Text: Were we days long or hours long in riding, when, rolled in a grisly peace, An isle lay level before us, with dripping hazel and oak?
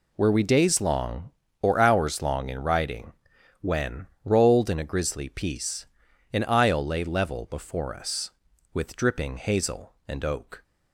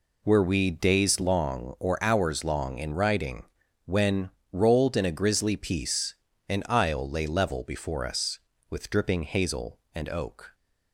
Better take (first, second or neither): neither